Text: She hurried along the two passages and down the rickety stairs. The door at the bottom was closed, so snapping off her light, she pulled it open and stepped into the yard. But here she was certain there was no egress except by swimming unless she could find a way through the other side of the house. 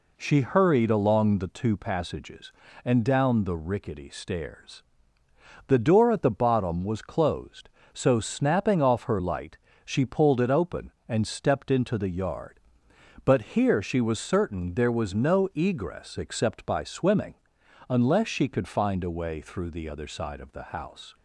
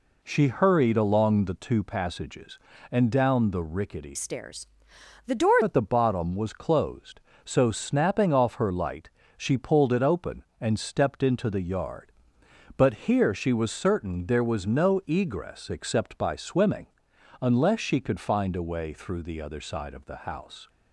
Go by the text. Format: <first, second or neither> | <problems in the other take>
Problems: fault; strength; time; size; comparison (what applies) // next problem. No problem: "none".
first | changes voice from "stairs" to "door"; from 4.1 to 5.5 s; 1.4 s long // pauses between "swimming" and "unless"; noticeable; at 16.8 s; 0.54 s long; noticeable in the first